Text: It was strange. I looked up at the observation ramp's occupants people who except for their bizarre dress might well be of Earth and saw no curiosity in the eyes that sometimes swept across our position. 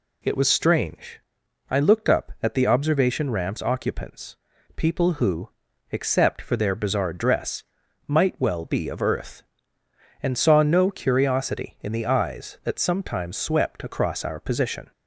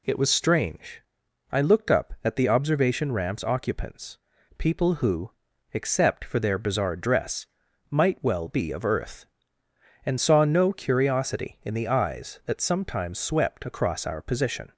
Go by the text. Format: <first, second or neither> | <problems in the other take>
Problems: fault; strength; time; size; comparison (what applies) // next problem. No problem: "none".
neither | pauses between "occupants" and "people"; the same in both // pauses between "who" and "except"; the same in both // pauses between "dress" and "might"; the same in both